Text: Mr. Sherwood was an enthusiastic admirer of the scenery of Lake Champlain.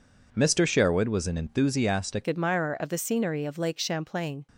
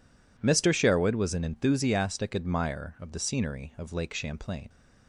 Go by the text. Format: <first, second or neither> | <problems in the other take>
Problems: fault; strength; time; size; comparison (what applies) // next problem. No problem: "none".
second | changes voice at "admirer"; from 2.2 s on; 2.2 s long